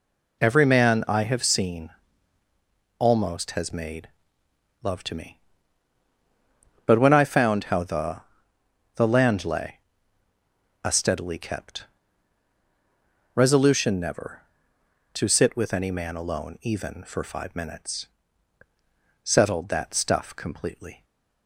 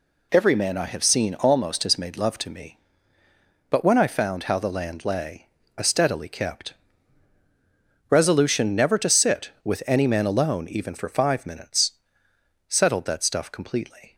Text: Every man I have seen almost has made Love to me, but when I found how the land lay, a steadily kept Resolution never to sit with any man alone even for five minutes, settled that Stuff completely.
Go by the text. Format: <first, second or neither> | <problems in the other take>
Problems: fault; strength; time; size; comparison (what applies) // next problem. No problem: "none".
second | pauses between "seen" and "almost"; at 1.9 s; 1.0 s long // pauses between "made" and "Love"; noticeable; at 4.0 s; 0.74 s long // says "the" twice; at 8.9 s // pauses between "kept" and "Resolution"; strong; at 11.8 s; 1.5 s long; strong in the second // stays silent after the last word; slight; from 20.9 s on; 0.5 s long